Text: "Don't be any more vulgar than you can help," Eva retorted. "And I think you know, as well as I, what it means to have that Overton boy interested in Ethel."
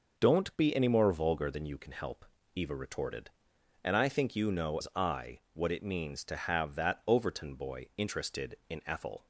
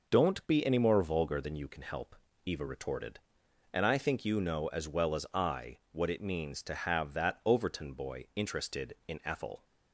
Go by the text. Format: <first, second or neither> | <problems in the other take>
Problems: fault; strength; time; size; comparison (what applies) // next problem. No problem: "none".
second | skips "as well"; at 4.7 s